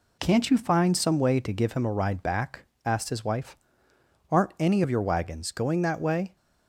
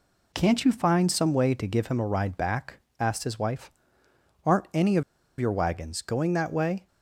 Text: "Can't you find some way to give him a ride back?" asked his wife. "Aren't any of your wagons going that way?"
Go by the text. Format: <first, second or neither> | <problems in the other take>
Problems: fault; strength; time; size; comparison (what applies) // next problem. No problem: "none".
first | pauses between "of" and "your"; slight; at 5.0 s; 0.35 s long